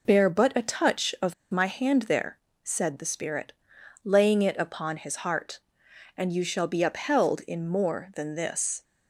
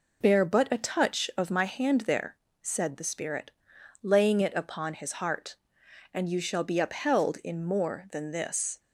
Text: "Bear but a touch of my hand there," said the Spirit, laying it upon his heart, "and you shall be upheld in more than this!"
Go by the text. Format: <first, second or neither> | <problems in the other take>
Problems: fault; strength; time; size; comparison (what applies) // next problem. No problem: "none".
second | pauses between "of" and "my"; slight; at 1.3 s; 0.17 s long